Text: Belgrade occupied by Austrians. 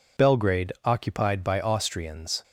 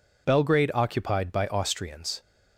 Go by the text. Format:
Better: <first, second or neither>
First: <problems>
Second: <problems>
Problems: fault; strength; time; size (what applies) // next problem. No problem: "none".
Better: neither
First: none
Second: none